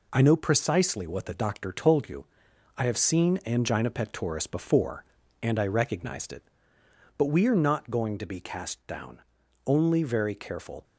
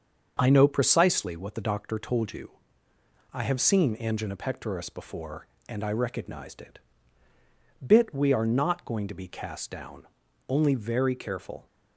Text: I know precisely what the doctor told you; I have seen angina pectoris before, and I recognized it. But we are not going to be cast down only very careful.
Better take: first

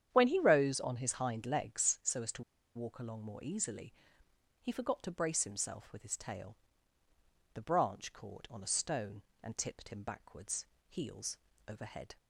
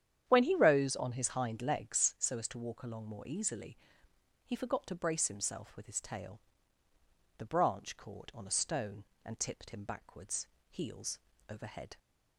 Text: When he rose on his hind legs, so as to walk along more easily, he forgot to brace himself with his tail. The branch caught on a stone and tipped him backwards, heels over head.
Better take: second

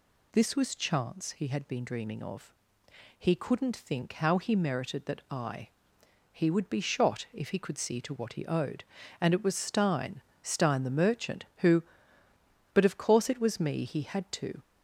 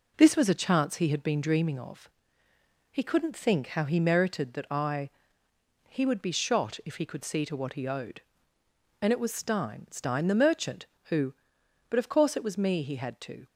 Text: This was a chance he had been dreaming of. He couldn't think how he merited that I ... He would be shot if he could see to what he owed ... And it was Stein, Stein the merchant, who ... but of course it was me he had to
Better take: second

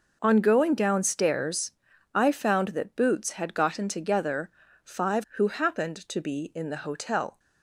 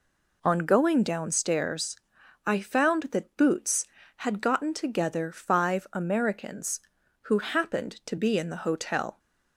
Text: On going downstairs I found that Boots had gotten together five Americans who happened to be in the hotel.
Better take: second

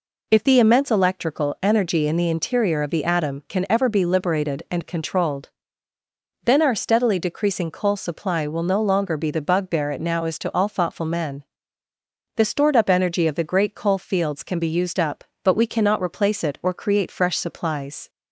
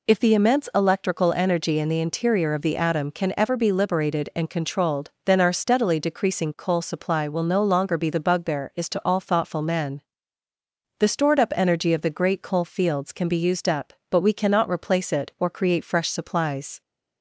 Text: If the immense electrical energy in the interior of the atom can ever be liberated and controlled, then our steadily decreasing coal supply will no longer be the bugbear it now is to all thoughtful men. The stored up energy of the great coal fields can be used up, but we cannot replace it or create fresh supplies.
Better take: first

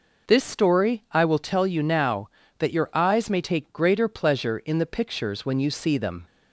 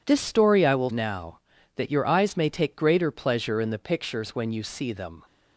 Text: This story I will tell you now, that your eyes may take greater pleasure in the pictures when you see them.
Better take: first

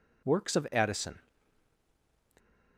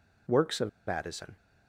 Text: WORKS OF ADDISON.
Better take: first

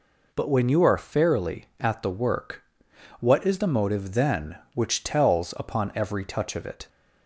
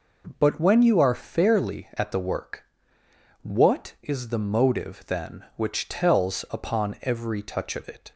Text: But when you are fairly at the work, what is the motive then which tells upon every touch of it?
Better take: neither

